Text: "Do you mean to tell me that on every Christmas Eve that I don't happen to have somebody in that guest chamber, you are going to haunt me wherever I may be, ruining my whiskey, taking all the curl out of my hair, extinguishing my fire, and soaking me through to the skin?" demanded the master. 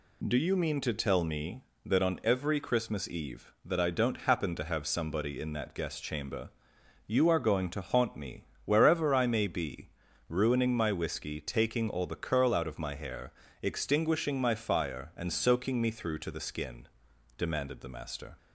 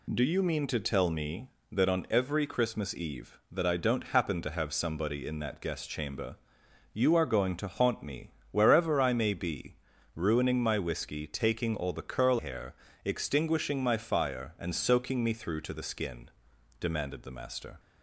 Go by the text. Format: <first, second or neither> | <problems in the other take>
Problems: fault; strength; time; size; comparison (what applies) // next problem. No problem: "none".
first | pauses between "me" and "wherever"; slight; at 8.3 s; 0.20 s long; slight in the first // skips "out of my"; at 12.3 s